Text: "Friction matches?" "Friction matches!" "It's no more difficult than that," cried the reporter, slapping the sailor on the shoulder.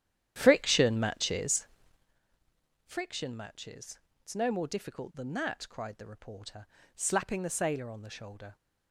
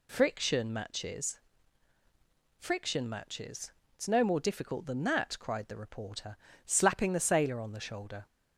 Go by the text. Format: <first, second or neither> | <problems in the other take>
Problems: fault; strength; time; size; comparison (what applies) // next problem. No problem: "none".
second | starts louder than the rest; strong; until 2.2 s; 11 dB